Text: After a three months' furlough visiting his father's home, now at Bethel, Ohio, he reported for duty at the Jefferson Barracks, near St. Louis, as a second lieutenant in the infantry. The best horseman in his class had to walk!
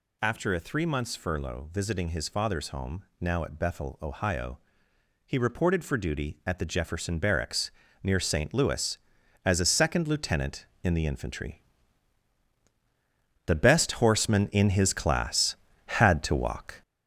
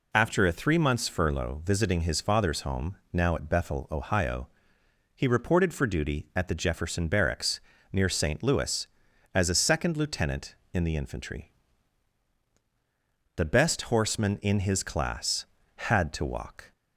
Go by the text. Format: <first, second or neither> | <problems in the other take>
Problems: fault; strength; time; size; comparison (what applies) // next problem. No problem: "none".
second | gets louder; noticeable; throughout; 6 dB